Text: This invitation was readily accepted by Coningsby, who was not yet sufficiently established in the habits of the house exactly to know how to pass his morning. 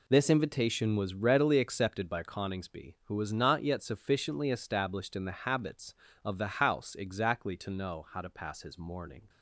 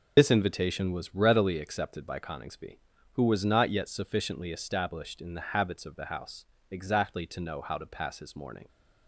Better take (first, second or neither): first